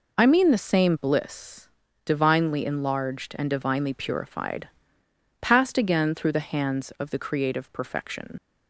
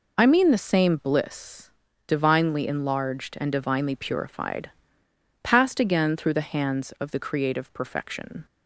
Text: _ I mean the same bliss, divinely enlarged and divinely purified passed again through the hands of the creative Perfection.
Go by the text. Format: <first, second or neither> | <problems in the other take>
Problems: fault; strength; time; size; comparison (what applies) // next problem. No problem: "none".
second | pauses between "purified" and "passed"; noticeable; at 4.6 s; 0.72 s long; noticeable in the second // leaves "Perfection" unfinished; at 8.3 s; 65 ms